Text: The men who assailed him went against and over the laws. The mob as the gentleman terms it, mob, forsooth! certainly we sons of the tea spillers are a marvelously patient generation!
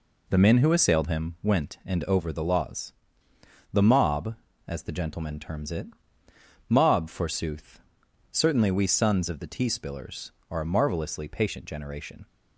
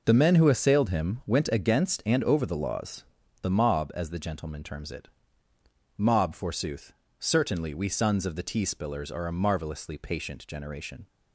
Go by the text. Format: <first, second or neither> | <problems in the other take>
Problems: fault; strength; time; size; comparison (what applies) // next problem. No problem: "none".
second | skips "against"; at 1.8 s